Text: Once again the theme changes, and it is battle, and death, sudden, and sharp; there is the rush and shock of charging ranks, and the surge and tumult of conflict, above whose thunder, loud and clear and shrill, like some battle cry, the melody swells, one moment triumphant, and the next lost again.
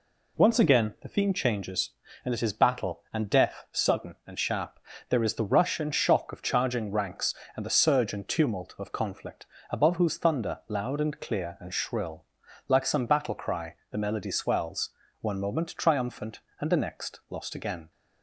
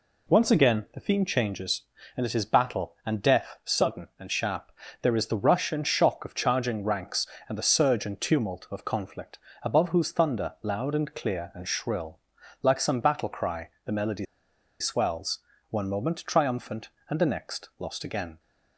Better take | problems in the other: first | pauses between "melody" and "swells"; noticeable; at 14.2 s; 0.55 s long

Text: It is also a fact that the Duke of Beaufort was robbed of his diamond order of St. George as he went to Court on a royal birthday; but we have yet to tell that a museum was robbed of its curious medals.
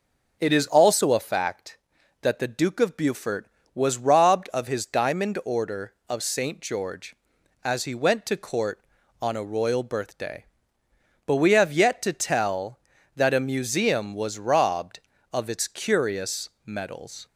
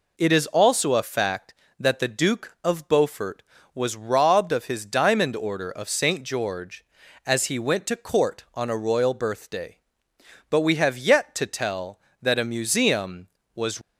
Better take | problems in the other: first | stops before "robbed of its curious medals"; at 13.8 s

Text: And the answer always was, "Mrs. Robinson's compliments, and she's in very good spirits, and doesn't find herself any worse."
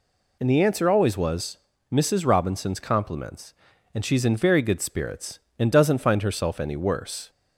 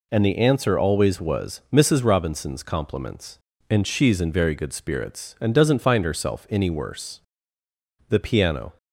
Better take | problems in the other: first | goes on to say "The piano"; noticeable; from 8.0 s on; 0.68 s long

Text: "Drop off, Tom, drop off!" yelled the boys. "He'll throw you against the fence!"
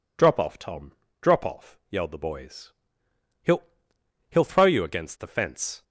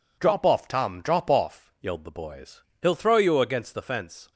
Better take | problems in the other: second | says "He'll" twice; at 4.2 s

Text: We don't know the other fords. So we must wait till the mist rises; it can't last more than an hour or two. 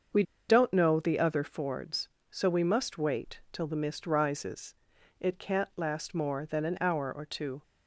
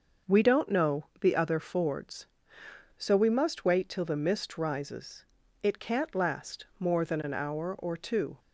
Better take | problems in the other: second | starts louder than the rest; until 1.4 s; 6.5 dB; noticeable in the second // pauses between "We" and "don't"; slight; at 0.2 s; 0.26 s long

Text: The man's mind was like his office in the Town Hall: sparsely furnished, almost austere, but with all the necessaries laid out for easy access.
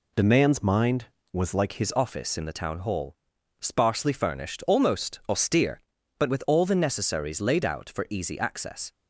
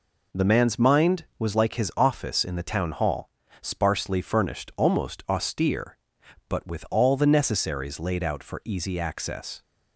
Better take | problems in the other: second | changes voice at "his"; from 1.7 s on; 7.2 s long

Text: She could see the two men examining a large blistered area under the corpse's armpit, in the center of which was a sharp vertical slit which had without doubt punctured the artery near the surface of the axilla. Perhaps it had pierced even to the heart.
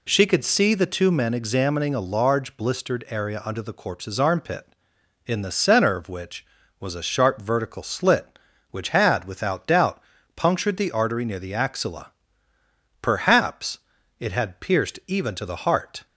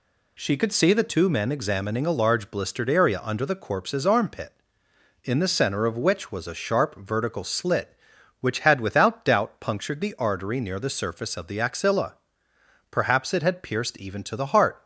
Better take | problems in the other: second | pauses between "doubt" and "punctured"; slight; at 10.0 s; 0.34 s long // skips "surface of the"; at 11.5 s // pauses between "Perhaps" and "it"; at 13.7 s; 0.38 s long

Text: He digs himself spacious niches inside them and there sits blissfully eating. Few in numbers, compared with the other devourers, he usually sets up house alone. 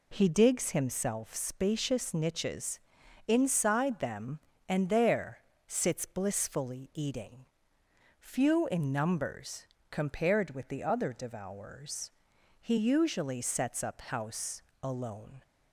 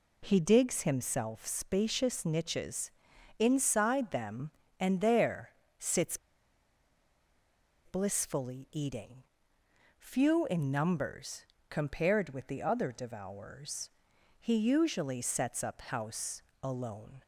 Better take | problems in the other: first | pauses between "niches" and "inside"; noticeable; at 2.8 s; 0.48 s long; noticeable in the first // pauses between "there" and "sits"; slight; at 5.4 s; 0.28 s long; slight in the first // pauses between "sits" and "blissfully"; strong; at 6.1 s; 1.6 s long // pauses between "house" and "alone"; slight; at 16.4 s; 0.20 s long; slight in the first

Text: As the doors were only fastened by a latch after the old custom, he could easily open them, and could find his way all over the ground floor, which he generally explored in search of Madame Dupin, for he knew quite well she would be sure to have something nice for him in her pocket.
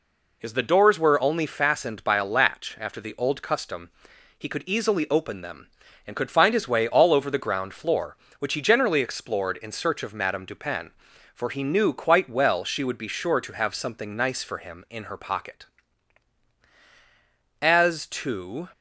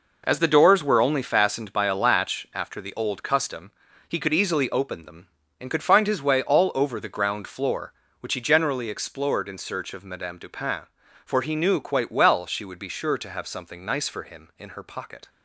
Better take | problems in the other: second | goes on to say "As to"; noticeable; from 17.6 s on; 1.0 s long

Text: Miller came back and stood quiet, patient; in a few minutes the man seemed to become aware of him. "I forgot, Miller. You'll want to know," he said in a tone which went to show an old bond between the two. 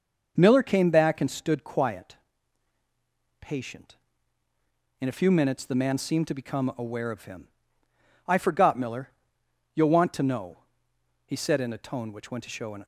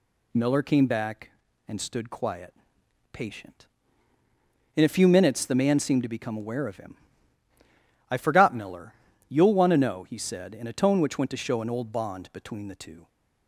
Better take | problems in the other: second | starts louder than the rest; noticeable; until 1.3 s; 6 dB // stops before "old bond between the two"; at 12.8 s

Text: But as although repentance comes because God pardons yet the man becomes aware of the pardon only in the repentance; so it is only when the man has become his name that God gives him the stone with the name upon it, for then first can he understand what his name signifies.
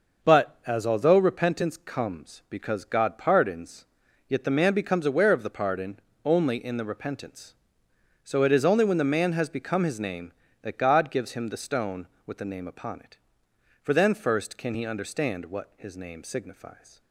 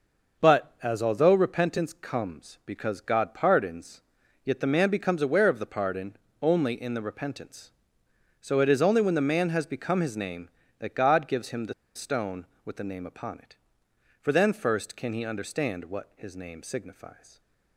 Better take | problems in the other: first | pauses between "pardons" and "yet"; at 4.0 s; 0.42 s long; also in the first // pauses between "pardon" and "only"; slight; at 6.1 s; 0.24 s long; slight in the first // pauses between "the" and "stone"; slight; at 11.7 s; 0.22 s long

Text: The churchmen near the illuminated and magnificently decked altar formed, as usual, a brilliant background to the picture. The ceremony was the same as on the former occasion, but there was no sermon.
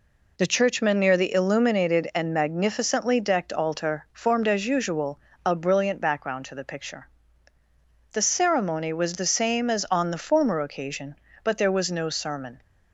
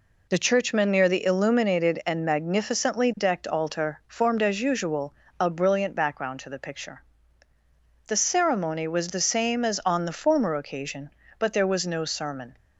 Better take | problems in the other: neither | none

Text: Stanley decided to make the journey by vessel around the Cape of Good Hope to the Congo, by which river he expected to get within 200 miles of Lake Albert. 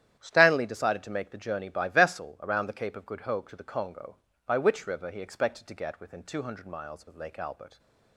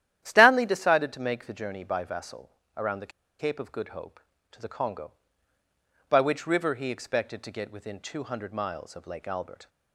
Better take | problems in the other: first | starts louder than the rest; strong; until 1.2 s; 11.5 dB; strong in the first // pauses between "vessel" and "around"; slight; at 2.4 s; 0.28 s long // pauses between "the" and "Cape"; slight; at 3.1 s; 0.28 s long

